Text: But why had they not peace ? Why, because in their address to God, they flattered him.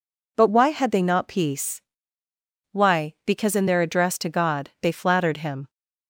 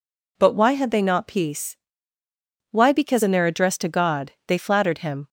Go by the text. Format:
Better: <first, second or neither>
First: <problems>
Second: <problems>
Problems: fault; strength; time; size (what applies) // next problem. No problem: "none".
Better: neither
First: none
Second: none